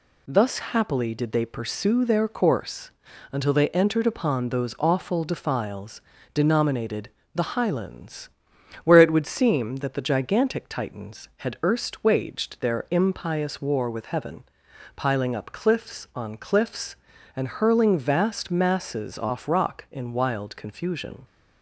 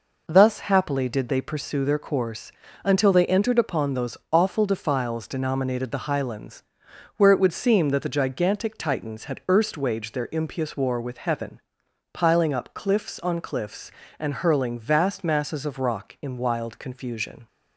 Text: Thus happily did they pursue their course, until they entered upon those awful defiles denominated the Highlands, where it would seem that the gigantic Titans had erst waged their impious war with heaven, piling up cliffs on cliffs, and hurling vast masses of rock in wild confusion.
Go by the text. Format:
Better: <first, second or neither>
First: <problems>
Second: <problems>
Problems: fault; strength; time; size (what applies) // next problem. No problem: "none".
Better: second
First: pauses between "defiles" and "denominated"; slight; at 5.9 s; 0.34 s long // pauses between "denominated" and "the"; slight; at 7.0 s; 0.24 s long // says "off" for "of"; at 19.1 s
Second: none